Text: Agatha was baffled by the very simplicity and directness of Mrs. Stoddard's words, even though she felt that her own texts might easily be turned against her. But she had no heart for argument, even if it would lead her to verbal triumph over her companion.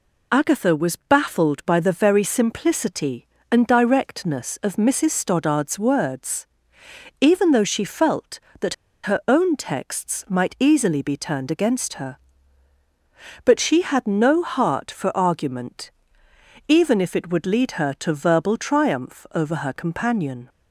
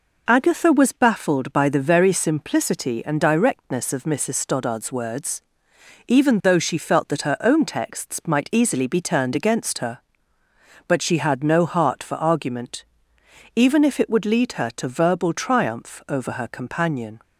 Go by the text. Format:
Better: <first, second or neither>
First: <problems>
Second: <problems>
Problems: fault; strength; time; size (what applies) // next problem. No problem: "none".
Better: second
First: pauses between "that" and "her"; slight; at 8.7 s; 0.29 s long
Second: none